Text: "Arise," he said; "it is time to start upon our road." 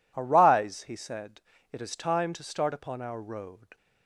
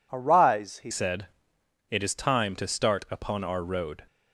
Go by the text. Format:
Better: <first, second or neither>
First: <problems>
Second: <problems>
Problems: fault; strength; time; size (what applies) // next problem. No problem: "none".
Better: first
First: none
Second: changes voice at "said"; from 0.9 s on; 3.1 s long